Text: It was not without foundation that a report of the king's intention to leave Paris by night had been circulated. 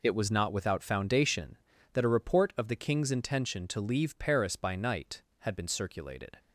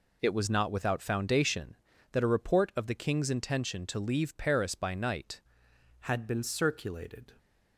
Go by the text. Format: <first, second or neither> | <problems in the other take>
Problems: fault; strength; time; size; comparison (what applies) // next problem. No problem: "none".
first | changes voice at "had"; from 6.0 s on; 1.3 s long